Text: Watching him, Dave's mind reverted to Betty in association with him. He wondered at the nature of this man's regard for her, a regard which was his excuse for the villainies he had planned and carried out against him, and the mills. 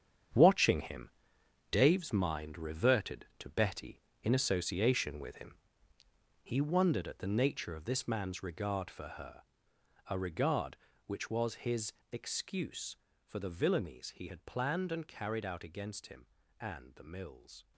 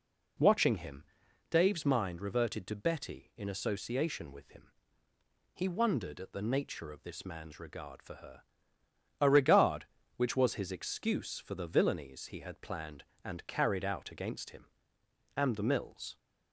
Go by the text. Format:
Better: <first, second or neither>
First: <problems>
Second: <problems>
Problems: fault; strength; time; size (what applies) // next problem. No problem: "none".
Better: second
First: gets quieter; strong; throughout; 10.5 dB // pauses between "his" and "excuse"; slight; at 11.9 s; 0.18 s long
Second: none